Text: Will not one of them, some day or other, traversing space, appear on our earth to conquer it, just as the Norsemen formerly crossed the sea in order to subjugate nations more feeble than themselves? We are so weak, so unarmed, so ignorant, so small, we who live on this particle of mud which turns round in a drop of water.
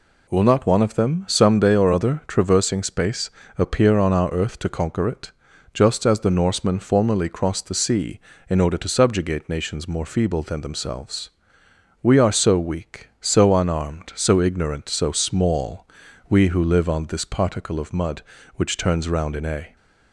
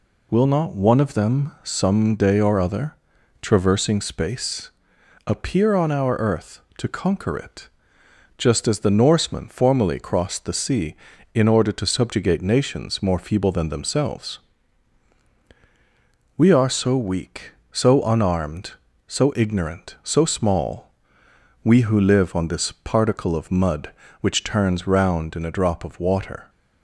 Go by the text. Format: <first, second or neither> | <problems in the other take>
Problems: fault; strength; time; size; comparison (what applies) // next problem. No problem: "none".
second | stops before "drop of water"; at 19.7 s